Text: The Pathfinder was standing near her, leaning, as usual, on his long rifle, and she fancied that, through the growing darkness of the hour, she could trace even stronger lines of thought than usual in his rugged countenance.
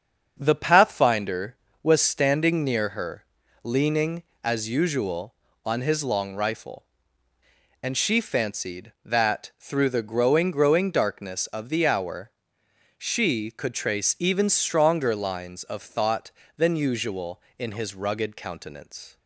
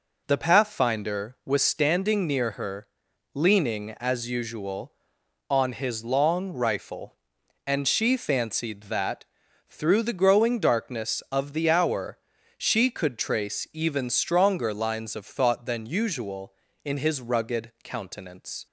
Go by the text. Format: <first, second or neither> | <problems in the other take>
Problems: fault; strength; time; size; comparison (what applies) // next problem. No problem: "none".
second | starts louder than the rest; until 1.4 s; 7 dB // says "growing" twice; at 10.5 s